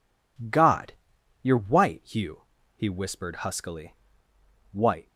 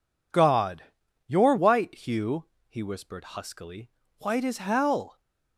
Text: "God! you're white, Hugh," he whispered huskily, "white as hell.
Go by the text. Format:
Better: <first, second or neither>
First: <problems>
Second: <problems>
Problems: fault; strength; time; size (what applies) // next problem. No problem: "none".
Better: second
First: stops before "as hell"; at 5.0 s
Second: none